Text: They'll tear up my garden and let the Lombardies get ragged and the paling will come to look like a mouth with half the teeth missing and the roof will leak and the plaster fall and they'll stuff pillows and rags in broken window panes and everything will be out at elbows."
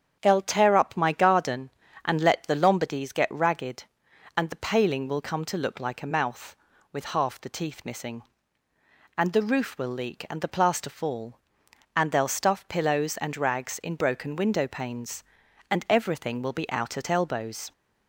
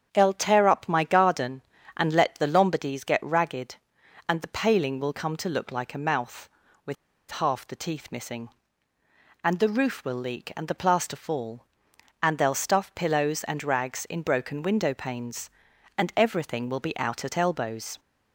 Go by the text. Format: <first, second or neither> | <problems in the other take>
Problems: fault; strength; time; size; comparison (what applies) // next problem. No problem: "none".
first | starts louder than the rest; strong; until 1.1 s; 8 dB; strong in the first // pauses between "with" and "half"; slight; at 6.9 s; 0.36 s long